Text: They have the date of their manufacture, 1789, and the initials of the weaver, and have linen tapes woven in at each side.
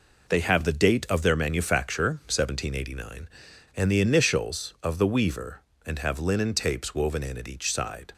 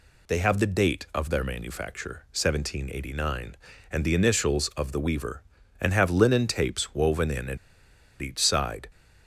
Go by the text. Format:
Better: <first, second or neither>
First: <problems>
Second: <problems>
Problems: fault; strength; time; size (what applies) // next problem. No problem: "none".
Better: first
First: none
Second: pauses between "at" and "each"; noticeable; at 7.5 s; 0.63 s long